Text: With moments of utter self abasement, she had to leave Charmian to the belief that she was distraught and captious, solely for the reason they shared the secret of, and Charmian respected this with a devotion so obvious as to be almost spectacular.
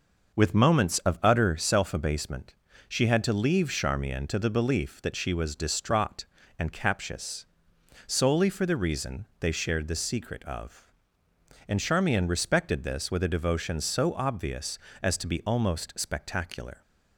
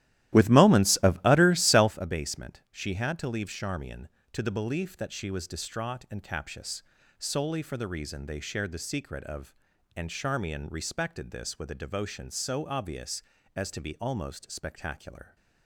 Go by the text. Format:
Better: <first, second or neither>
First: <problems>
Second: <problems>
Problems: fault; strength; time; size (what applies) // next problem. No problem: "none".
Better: first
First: none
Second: starts louder than the rest; strong; until 2.0 s; 14 dB